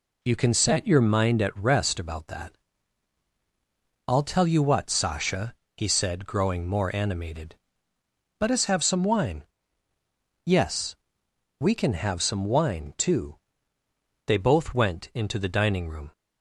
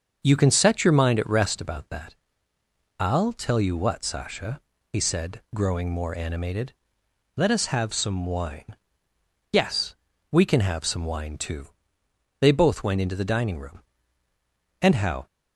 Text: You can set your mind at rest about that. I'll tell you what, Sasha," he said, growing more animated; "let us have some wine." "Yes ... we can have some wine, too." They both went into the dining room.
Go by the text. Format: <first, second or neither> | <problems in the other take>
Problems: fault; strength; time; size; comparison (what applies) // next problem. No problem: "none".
first | starts louder than the rest; until 1.2 s; 6.5 dB // goes on to say "And how"; slight; from 14.8 s on; 0.46 s long